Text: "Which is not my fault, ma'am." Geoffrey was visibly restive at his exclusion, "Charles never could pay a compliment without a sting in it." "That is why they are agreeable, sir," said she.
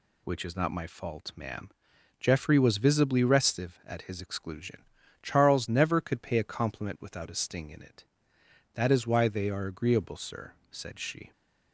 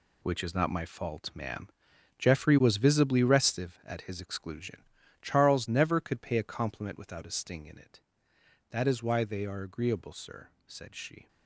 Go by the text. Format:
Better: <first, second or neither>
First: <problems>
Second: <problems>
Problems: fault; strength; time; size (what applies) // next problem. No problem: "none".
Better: first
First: none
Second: gets quieter; strong; throughout; 9.5 dB